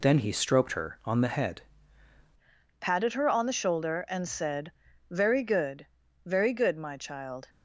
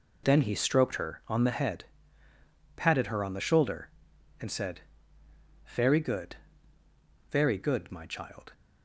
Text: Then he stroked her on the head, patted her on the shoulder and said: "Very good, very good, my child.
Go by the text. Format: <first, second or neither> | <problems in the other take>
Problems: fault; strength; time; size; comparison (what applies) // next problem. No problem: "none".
second | changes voice at "patted"; from 2.7 s on; 4.7 s long